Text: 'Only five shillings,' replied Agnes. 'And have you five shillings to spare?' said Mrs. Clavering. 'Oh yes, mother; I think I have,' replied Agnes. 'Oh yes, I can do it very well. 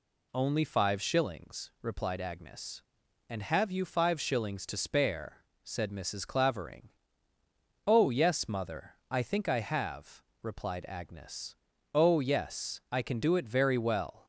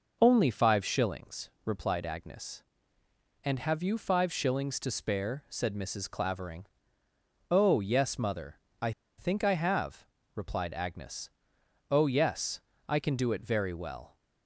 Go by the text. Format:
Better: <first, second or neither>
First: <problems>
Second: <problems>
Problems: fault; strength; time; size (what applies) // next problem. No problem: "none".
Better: first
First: none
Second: pauses between "I" and "think"; slight; at 8.9 s; 0.27 s long